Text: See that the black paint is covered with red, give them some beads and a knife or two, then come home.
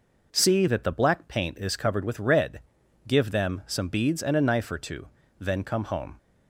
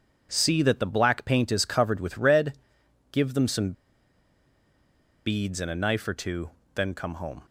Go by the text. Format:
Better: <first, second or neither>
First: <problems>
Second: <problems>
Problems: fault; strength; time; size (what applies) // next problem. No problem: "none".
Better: first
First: none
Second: pauses between "some" and "beads"; strong; at 3.7 s; 1.5 s long